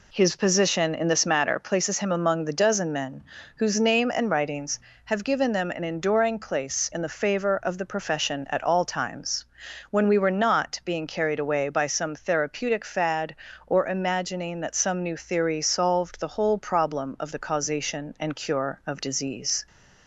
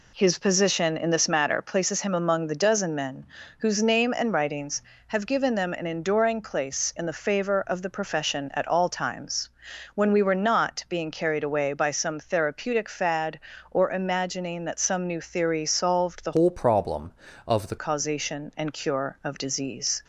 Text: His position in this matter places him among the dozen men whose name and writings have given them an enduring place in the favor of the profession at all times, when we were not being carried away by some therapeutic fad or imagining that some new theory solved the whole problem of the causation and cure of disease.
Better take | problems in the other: first | pauses between "men" and "whose"; slight; at 3.2 s; 0.32 s long; slight in the first // changes voice from "whole" to "the"; from 16.3 to 17.7 s; 1.4 s long

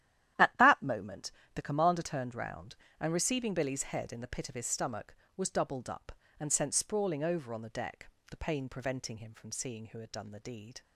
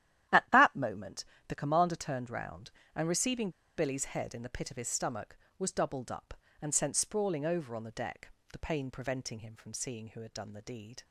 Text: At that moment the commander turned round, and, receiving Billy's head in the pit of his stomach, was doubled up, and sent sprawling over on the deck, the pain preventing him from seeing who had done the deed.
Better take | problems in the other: first | starts louder than the rest; strong; until 1.5 s; 12 dB; strong in the first // pauses between "moment" and "the"; slight; at 1.2 s; 0.24 s long; slight in the first // pauses between "receiving" and "Billy's"; slight; at 3.4 s; 0.27 s long

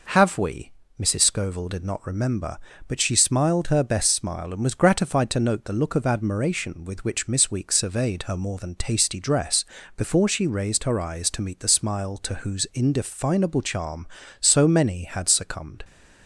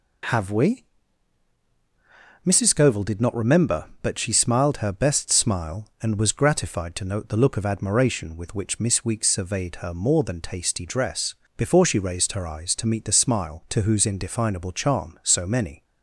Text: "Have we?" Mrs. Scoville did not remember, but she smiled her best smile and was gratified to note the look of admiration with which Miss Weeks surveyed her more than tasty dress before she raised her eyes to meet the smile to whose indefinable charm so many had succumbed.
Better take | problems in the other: first | pauses between "dress" and "before"; slight; at 11.3 s; 0.24 s long; slight in the first // stops before "had succumbed"; at 15.8 s

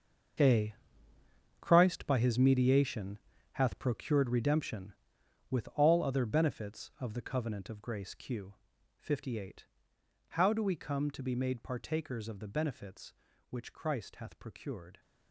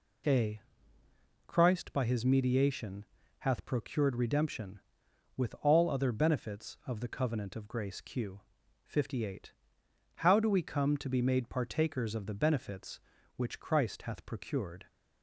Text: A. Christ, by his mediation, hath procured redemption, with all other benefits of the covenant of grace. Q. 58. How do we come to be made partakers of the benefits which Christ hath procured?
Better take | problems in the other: second | gets quieter; strong; throughout; 13.5 dB

